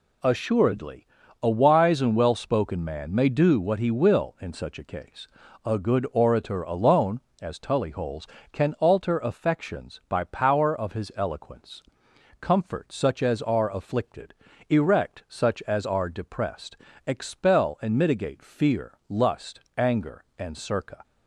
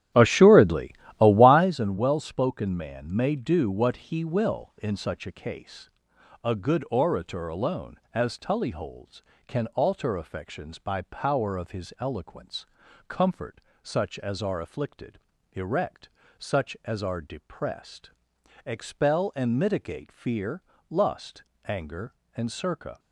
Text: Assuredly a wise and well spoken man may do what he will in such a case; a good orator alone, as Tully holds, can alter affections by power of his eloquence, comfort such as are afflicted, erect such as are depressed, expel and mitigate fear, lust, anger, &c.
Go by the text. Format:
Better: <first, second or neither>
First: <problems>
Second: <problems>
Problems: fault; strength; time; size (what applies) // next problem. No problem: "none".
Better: first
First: pauses between "Assuredly" and "a"; at 1.0 s; 0.38 s long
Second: starts louder than the rest; strong; until 1.7 s; 12 dB // pauses between "Assuredly" and "a"; slight; at 0.9 s; 0.28 s long // pauses between "comfort" and "such"; slight; at 13.6 s; 0.22 s long // pauses between "erect" and "such"; slight; at 16.0 s; 0.30 s long